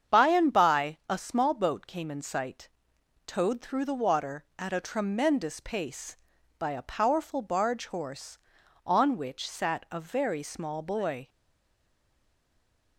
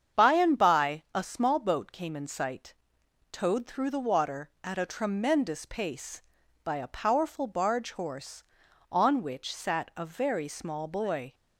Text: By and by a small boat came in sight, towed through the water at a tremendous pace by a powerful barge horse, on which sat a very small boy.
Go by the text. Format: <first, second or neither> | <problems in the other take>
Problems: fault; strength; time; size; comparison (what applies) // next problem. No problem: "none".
second | starts louder than the rest; strong; until 1.2 s; 7.5 dB; strong in the second // stays silent after the last word; noticeable; from 11.2 s on; 1.7 s long